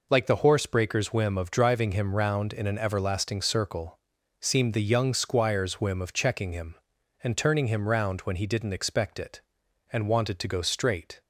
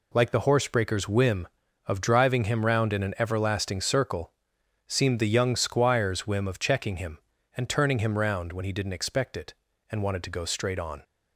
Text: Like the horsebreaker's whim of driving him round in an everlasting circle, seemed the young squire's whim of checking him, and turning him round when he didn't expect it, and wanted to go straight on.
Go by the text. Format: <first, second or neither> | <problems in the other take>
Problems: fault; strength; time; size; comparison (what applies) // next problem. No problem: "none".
second | stops before "on"; at 11.2 s